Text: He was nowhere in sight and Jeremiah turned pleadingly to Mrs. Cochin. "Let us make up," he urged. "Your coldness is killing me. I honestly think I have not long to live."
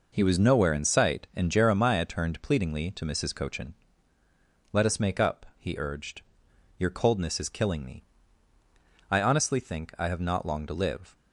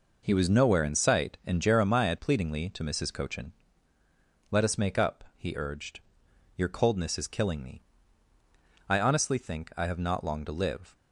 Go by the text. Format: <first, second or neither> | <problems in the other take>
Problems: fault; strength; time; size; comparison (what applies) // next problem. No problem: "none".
first | skips "turned"; at 2.1 s